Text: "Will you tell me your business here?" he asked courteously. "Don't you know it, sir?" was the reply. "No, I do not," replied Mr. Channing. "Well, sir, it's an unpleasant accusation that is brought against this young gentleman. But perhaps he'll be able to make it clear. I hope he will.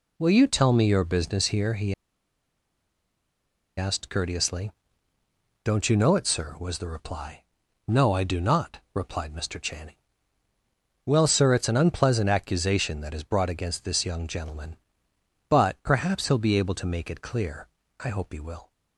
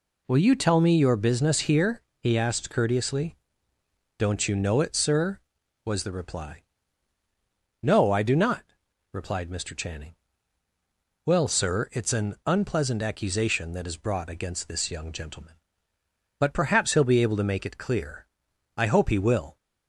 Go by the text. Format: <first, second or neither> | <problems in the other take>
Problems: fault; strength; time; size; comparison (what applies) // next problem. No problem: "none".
second | pauses between "he" and "asked"; strong; at 1.9 s; 1.8 s long